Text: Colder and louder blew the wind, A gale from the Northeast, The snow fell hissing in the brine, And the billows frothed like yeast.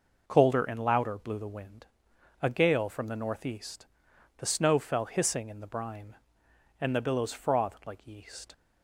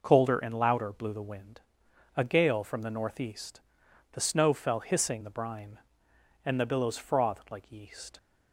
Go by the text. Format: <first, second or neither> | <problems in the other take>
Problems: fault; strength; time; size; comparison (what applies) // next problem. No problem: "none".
first | skips "in"; at 5.2 s